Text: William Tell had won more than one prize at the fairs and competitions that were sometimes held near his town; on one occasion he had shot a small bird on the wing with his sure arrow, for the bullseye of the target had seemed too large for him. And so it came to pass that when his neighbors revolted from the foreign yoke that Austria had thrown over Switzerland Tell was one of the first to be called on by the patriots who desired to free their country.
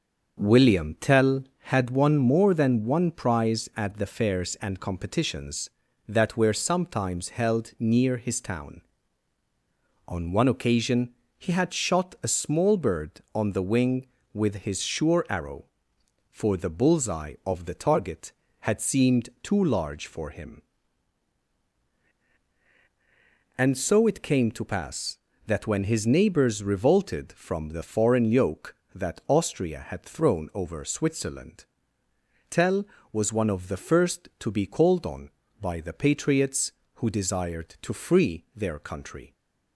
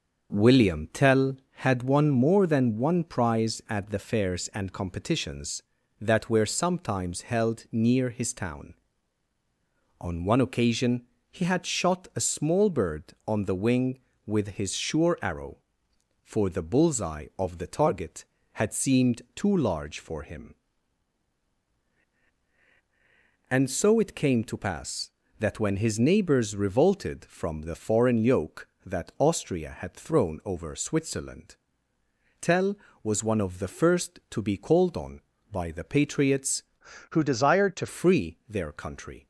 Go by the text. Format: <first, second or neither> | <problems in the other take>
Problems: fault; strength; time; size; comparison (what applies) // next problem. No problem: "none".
first | starts louder than the rest; until 1.5 s; 6.5 dB; also in the first // pauses between "occasion" and "he"; slight; at 11.0 s; 0.24 s long; slight in the first // pauses between "Switzerland" and "Tell"; noticeable; at 31.5 s; 0.86 s long; noticeable in the first // changes voice from "who" to "to"; from 37.1 to 37.8 s; 0.7 s long